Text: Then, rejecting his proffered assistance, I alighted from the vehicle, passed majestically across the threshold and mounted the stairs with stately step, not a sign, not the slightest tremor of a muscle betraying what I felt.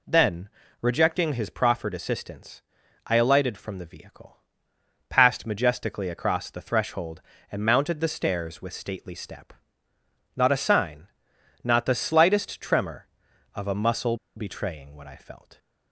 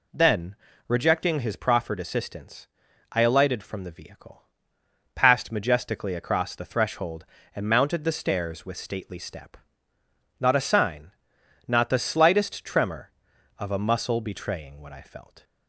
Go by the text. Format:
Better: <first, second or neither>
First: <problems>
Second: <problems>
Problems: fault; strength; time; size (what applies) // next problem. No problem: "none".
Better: second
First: pauses between "muscle" and "betraying"; slight; at 14.1 s; 0.20 s long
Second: none